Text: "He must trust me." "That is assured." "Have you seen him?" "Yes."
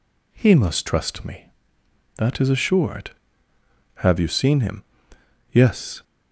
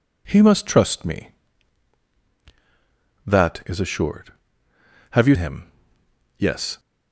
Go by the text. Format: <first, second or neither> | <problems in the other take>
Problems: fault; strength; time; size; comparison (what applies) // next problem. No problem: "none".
first | skips "seen"; at 5.3 s